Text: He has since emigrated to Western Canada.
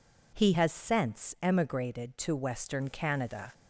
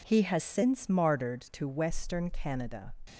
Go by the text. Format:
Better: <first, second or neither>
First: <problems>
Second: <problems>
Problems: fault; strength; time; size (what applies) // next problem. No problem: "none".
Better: first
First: none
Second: says "martyred" for "emigrated"; at 0.8 s